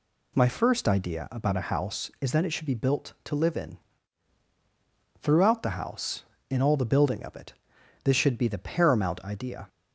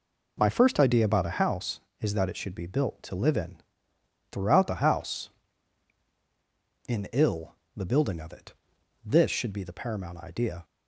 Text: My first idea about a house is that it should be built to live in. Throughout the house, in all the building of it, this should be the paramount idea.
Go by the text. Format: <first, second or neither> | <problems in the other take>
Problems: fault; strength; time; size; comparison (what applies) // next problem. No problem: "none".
first | says "ill" for "all"; at 7.1 s